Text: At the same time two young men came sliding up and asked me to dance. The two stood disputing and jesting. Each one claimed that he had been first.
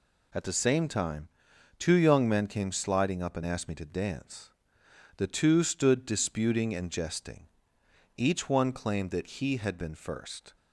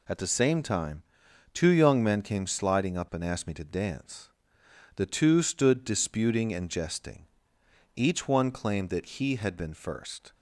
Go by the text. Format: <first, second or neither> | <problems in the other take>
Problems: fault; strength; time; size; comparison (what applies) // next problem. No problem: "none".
neither | pauses between "time" and "two"; noticeable; the same in both